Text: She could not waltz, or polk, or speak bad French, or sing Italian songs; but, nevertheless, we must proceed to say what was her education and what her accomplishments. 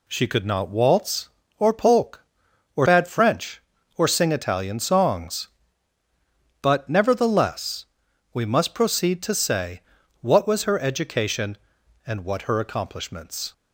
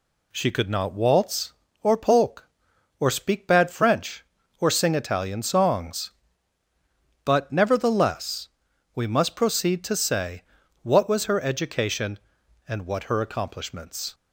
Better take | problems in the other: second | skips "speak"; at 2.8 s // pauses between "say" and "what"; at 9.8 s; 0.40 s long; also in the second

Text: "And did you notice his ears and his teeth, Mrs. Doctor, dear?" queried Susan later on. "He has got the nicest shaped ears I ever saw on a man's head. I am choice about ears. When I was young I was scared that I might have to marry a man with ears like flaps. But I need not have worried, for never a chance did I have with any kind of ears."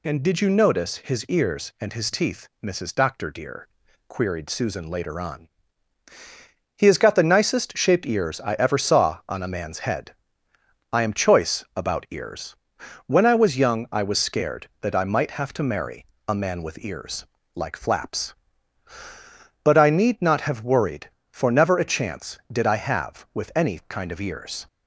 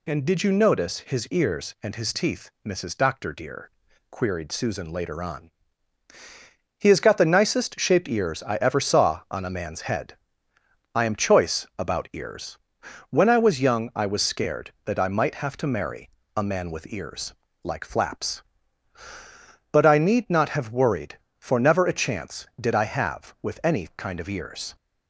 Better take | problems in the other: neither | pauses between "marry" and "a"; slight; the same in both // pauses between "ears" and "like"; slight; the same in both

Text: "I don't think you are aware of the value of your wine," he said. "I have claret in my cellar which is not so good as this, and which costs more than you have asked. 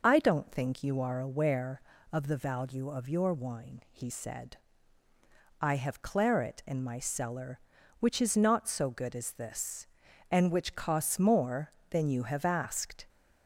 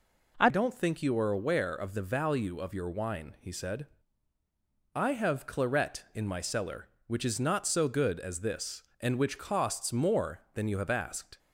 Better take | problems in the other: first | changes voice at "don't"; from 0.4 s on; 10.9 s long

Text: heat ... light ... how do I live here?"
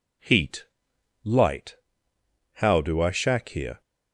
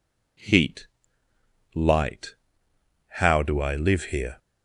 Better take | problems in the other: second | says "shack" for "live"; at 3.1 s

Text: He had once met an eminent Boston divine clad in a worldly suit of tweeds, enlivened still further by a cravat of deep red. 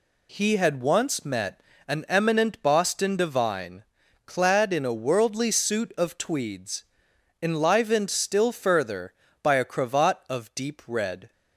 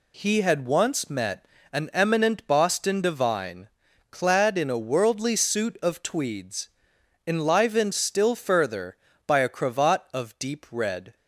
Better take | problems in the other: neither | pauses between "met" and "an"; slight; the same in both // pauses between "divine" and "clad"; the same in both

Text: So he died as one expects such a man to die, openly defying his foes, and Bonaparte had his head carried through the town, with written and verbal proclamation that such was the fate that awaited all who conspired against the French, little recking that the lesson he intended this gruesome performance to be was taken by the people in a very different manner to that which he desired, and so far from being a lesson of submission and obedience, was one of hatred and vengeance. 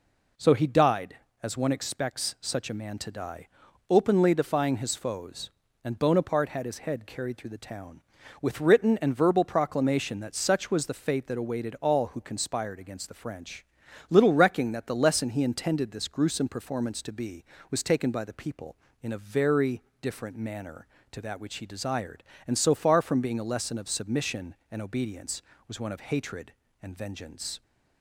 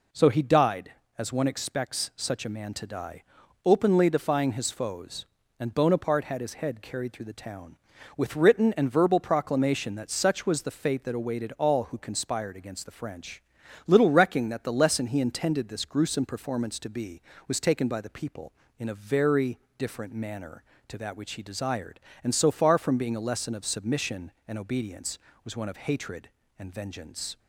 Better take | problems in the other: neither | pauses between "very" and "different"; slight; the same in both

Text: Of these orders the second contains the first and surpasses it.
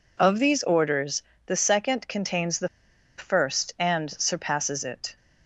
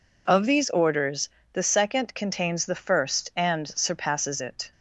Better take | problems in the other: second | pauses between "orders" and "the"; slight; at 1.2 s; 0.24 s long; slight in the second // pauses between "the" and "first"; noticeable; at 2.6 s; 0.51 s long

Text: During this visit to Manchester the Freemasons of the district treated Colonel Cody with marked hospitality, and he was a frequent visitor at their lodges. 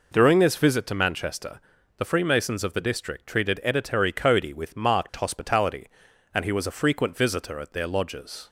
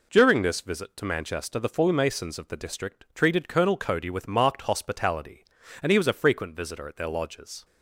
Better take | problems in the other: second | pauses between "Manchester" and "the"; at 1.5 s; 0.38 s long // says "Editary" for "Colonel"; at 3.6 s

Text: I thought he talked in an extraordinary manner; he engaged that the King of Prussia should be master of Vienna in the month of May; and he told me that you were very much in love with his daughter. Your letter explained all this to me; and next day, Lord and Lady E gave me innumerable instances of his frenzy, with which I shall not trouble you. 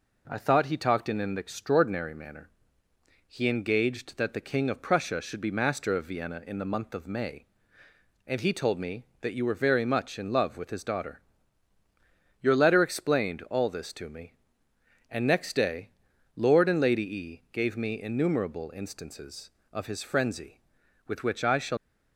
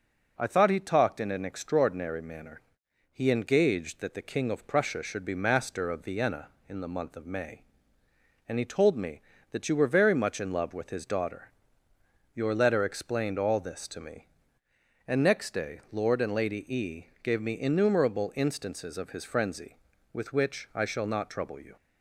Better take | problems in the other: second | stops before "not trouble you"; at 21.7 s

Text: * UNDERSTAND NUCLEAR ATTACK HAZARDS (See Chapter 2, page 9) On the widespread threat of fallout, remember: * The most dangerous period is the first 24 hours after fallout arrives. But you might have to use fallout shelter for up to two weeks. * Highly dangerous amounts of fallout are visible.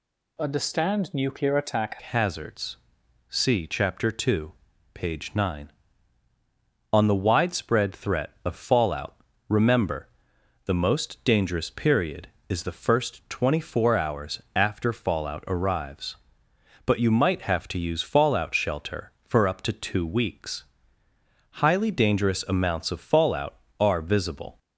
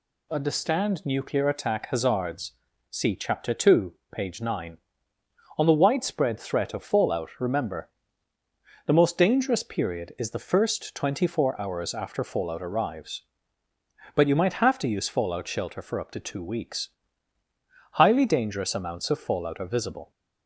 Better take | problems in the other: second | changes voice at "HAZARDS"; from 2.0 s on; 22.5 s long

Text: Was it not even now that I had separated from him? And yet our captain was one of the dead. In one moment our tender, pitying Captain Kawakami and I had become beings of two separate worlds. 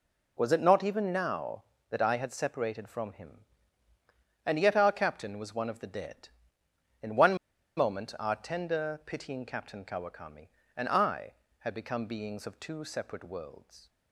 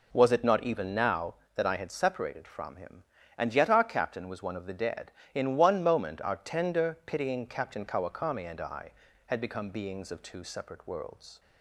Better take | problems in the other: second | pauses between "one" and "moment"; at 7.3 s; 0.41 s long

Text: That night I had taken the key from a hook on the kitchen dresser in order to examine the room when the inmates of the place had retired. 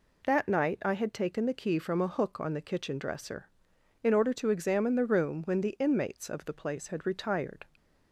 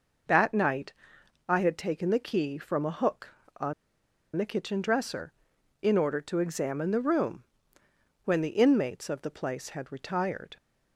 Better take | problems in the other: first | pauses between "night" and "I"; noticeable; at 0.9 s; 0.56 s long // pauses between "on" and "the"; noticeable; at 3.7 s; 0.63 s long // pauses between "room" and "when"; noticeable; at 7.4 s; 0.80 s long

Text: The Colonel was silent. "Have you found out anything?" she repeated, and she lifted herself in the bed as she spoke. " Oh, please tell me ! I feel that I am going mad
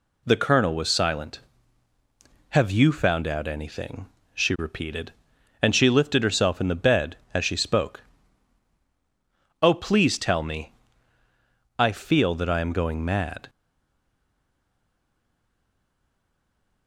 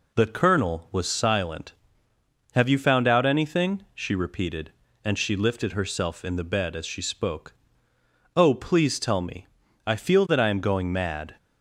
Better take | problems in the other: second | stays silent after the last word; strong; from 13.4 s on; 3.4 s long

